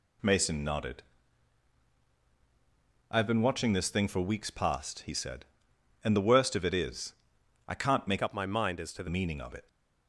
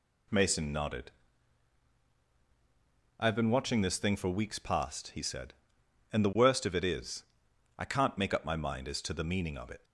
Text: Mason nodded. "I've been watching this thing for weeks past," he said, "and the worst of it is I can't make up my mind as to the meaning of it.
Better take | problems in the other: second | pauses between "is" and "I"; noticeable; at 7.1 s; 0.54 s long; noticeable in the second // changes voice from "up" to "the"; from 8.2 to 9.0 s; 0.8 s long

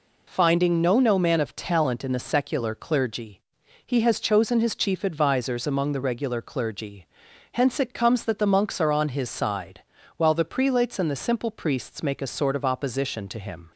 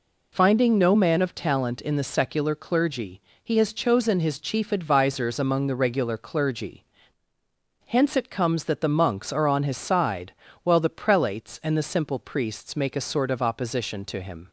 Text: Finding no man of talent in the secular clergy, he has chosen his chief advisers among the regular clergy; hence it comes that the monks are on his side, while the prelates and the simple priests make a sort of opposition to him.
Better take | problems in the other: second | says "no" twice; at 1.0 s

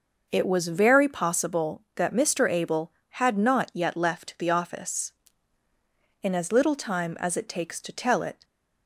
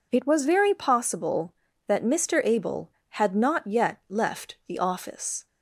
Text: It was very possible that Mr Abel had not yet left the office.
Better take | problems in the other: second | goes on to say "In as little time as it takes to tell it"; strong; from 6.2 s on; 2.2 s long

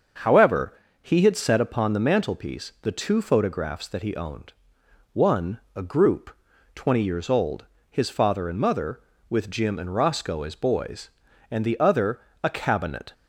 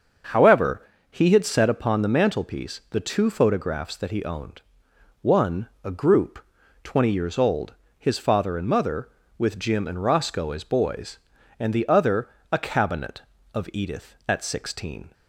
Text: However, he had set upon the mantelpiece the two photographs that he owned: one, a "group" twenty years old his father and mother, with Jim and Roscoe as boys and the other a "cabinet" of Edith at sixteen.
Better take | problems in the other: second | starts louder than the rest; until 1.5 s; 6.5 dB; also in the second // pauses between "group" and "twenty"; at 6.3 s; 0.40 s long; also in the second // pauses between "old" and "his"; slight; at 7.6 s; 0.24 s long; slight in the second // pauses between "other" and "a"; slight; at 12.1 s; 0.24 s long; slight in the second // stops before "of Edith at sixteen"; at 13.1 s

